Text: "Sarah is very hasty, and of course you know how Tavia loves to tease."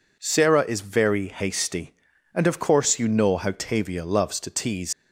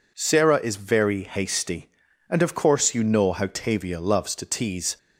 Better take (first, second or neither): second